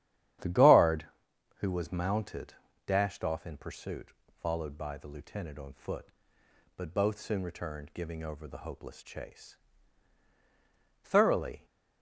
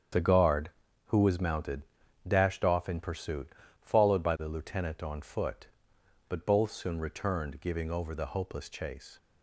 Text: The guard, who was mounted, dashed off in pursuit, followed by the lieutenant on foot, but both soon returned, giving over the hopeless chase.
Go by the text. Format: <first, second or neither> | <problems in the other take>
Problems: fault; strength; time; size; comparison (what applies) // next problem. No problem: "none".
second | starts louder than the rest; strong; until 1.9 s; 10.5 dB; strong in the second // goes on to say "Thoroughly"; noticeable; from 11.0 s on; 0.62 s long